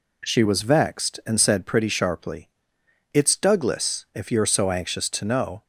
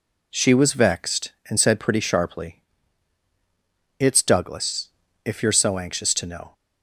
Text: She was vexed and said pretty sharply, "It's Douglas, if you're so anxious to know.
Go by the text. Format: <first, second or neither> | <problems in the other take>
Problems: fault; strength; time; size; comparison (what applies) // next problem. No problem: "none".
neither | none